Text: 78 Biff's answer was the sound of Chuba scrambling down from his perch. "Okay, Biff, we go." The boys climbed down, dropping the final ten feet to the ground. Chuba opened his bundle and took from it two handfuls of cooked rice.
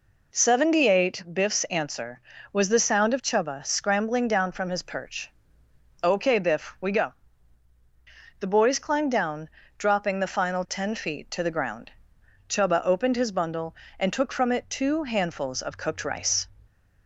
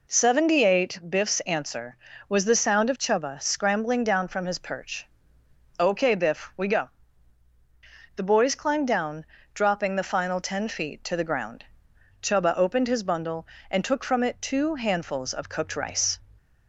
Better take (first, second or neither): neither